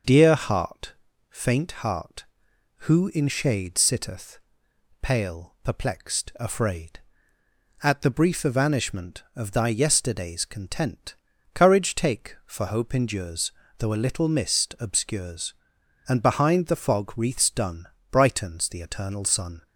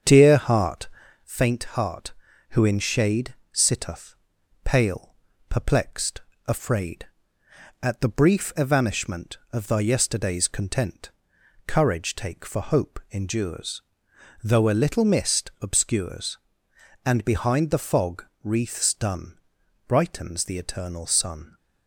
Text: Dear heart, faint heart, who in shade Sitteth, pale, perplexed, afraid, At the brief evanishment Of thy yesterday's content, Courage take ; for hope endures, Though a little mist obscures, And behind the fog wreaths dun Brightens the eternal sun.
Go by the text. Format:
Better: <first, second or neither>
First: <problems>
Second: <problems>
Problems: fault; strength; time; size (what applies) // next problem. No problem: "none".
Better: first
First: pauses between "dun" and "Brightens"; slight; at 17.8 s; 0.24 s long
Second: starts louder than the rest; strong; until 1.3 s; 7.5 dB // pauses between "shade" and "Sitteth"; slight; at 3.3 s; 0.18 s long // pauses between "fog" and "wreaths"; slight; at 18.2 s; 0.18 s long // pauses between "dun" and "Brightens"; noticeable; at 19.3 s; 0.50 s long